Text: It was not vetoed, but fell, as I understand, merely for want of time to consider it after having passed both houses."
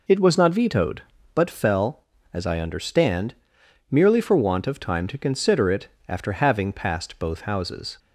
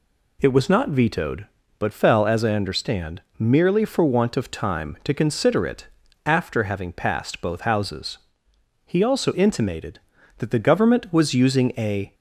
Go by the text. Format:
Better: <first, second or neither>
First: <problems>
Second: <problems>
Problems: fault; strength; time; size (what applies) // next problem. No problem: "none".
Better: first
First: pauses between "it" and "after"; slight; at 5.8 s; 0.18 s long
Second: pauses between "it" and "after"; at 5.8 s; 0.38 s long // goes on to say "He also intimated that the Government was using a"; strong; from 8.8 s on; 3.2 s long